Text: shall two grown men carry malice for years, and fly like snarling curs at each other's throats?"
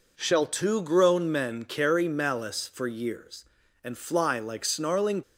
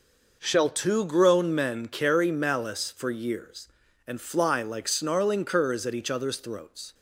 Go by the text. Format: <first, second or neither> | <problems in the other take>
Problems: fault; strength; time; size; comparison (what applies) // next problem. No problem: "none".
second | stops before "curs at each other's throats"; at 5.2 s